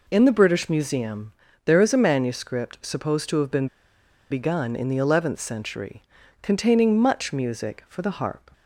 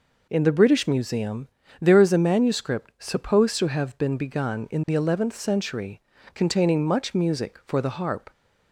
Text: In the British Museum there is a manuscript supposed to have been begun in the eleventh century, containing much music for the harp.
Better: second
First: pauses between "Museum" and "there"; slight; at 1.3 s; 0.34 s long // pauses between "been" and "begun"; noticeable; at 3.6 s; 0.64 s long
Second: pauses between "Museum" and "there"; slight; at 1.4 s; 0.32 s long

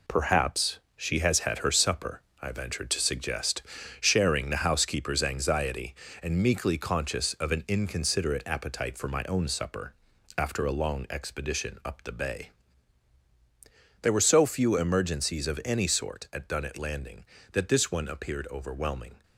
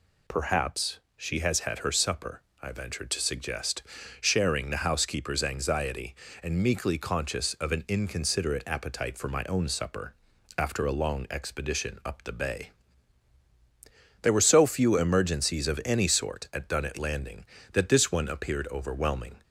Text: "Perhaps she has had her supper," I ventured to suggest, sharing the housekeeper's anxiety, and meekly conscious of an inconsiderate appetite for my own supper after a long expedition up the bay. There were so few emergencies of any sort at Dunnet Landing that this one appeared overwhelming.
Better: second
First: gets quieter; strong; throughout; 8 dB // pauses between "Perhaps" and "she"; slight; at 0.7 s; 0.18 s long // pauses between "supper" and "after"; at 9.9 s; 0.42 s long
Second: pauses between "Perhaps" and "she"; slight; at 0.9 s; 0.18 s long // pauses between "supper" and "after"; at 10.1 s; 0.42 s long

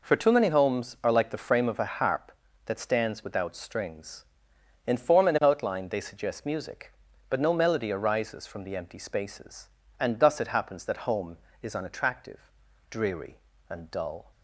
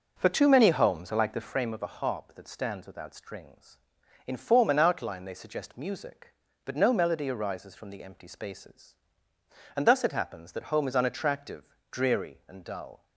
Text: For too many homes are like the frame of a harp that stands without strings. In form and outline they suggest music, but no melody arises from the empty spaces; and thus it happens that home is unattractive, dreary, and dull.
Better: first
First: none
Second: starts louder than the rest; noticeable; until 1.6 s; 6 dB

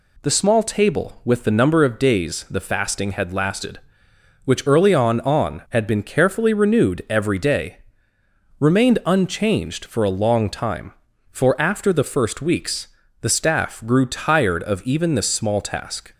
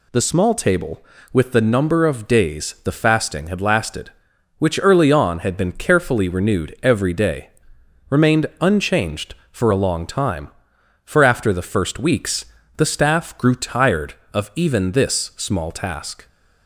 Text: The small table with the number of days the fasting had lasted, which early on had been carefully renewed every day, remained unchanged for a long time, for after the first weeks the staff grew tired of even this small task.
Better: second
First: says "on" twice; at 5.2 s // pauses between "weeks" and "the"; slight; at 12.8 s; 0.34 s long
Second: pauses between "weeks" and "the"; slight; at 12.4 s; 0.32 s long

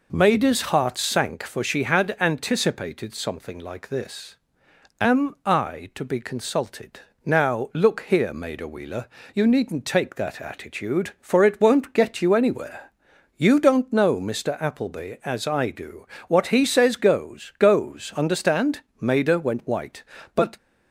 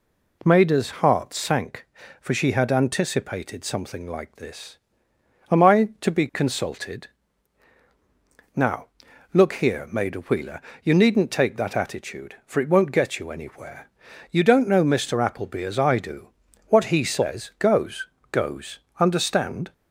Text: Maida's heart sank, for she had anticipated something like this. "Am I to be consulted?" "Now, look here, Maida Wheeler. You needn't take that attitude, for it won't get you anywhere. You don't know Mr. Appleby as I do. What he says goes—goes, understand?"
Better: second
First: goes on to say "Maida went white But"; from 19.0 s on; 1.5 s long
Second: none

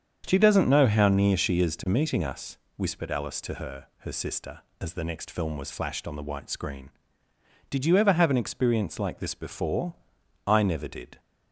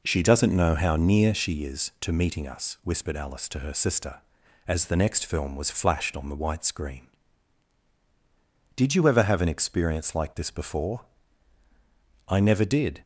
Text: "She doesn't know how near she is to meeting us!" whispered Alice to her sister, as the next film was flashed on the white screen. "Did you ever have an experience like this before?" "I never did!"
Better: second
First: starts louder than the rest; strong; until 1.2 s; 7 dB // says "her" twice; at 3.9 s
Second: none

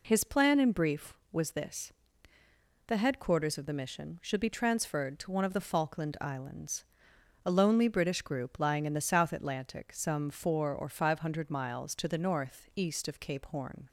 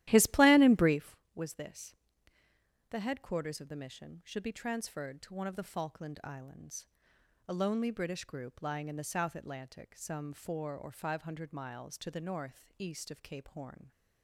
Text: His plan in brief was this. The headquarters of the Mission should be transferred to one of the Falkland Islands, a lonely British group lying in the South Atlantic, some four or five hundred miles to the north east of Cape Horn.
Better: first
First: none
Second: starts louder than the rest; strong; until 1.1 s; 14.5 dB

